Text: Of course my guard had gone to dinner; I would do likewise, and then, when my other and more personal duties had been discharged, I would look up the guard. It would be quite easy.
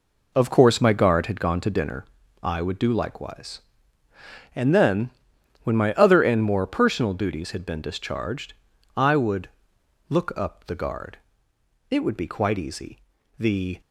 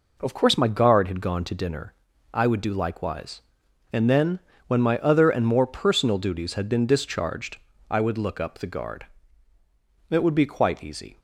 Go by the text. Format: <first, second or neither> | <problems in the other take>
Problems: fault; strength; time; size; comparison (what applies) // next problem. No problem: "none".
second | pauses between "would" and "look"; noticeable; at 9.4 s; 0.60 s long // goes on to say "The"; slight; from 13.4 s on; 0.40 s long